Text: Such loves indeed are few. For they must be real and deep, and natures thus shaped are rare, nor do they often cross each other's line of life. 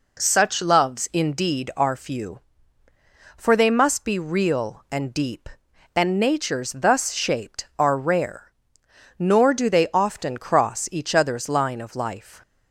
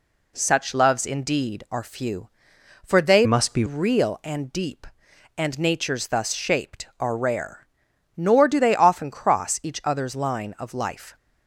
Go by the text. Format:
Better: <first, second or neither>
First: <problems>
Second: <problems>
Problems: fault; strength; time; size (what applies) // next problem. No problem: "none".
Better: first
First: none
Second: changes voice from "must" to "be"; from 3.2 to 3.6 s; 0.4 s long